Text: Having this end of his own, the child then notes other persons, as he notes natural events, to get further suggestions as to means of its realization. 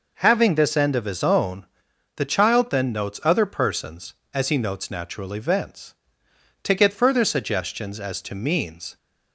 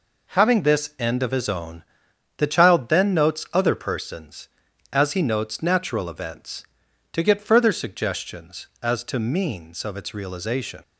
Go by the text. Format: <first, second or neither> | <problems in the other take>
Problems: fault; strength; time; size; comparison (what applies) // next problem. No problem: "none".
second | stops before "of its realization"; at 8.9 s